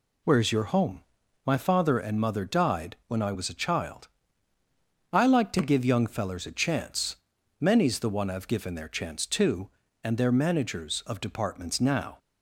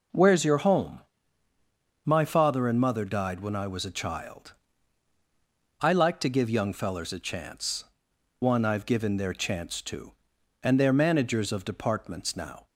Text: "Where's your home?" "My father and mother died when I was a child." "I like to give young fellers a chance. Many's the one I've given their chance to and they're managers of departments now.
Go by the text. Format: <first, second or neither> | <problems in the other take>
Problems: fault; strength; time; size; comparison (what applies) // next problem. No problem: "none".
first | skips "Many's the"; at 8.1 s